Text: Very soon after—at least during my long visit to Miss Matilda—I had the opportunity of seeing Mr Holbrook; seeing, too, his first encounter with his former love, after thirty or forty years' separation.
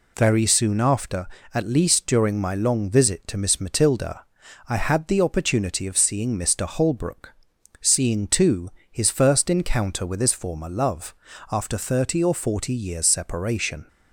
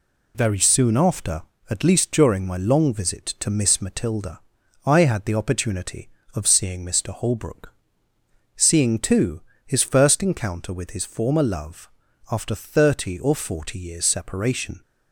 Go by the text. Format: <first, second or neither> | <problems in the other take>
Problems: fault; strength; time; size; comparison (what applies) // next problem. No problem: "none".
neither | none